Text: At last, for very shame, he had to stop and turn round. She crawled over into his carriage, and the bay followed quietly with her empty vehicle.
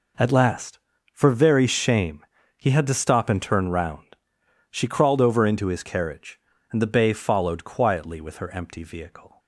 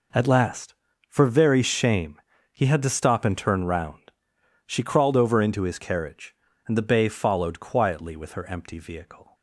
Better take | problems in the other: neither | none

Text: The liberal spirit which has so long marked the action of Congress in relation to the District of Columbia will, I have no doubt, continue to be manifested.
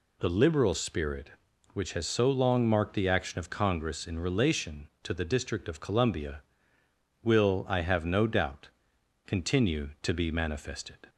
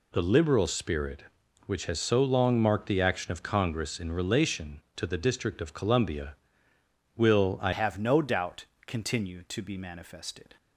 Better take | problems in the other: first | changes voice at "have"; from 7.7 s on; 2.8 s long

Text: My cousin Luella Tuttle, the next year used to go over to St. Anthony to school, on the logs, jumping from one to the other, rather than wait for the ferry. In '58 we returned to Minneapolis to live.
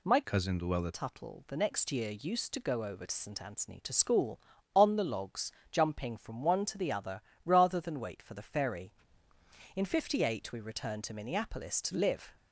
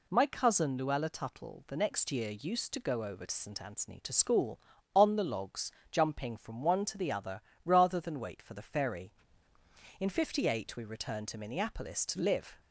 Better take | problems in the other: second | changes voice from "cousin" to "Luella"; from 0.2 to 0.9 s; 0.7 s long

